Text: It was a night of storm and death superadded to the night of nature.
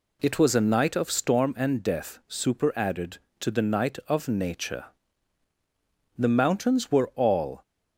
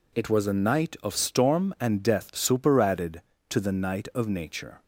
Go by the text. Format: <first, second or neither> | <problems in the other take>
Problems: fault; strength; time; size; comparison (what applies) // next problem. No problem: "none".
second | goes on to say "The mountains were all"; from 6.1 s on; 1.4 s long